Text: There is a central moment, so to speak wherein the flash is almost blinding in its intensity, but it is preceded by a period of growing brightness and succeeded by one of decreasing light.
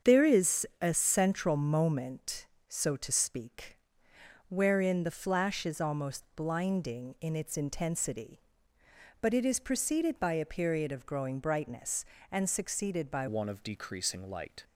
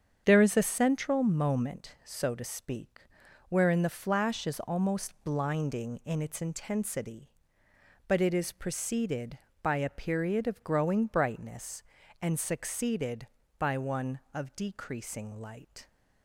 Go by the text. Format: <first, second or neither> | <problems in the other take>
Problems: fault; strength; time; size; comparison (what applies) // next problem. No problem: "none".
second | starts louder than the rest; strong; until 1.1 s; 7.5 dB; strong in the second // pauses between "speak" and "wherein"; noticeable; at 3.7 s; 0.70 s long; noticeable in the second // changes voice at "one"; from 13.2 s on; 1.4 s long